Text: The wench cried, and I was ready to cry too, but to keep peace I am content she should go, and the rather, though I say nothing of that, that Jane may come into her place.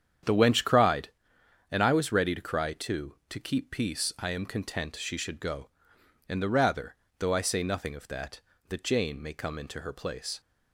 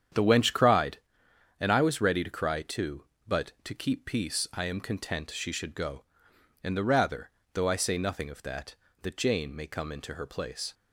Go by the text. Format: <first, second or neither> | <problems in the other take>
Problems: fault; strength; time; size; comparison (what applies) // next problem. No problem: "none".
second | starts louder than the rest; strong; until 1.8 s; 8.5 dB; strong in the second // skips "but"; at 3.2 s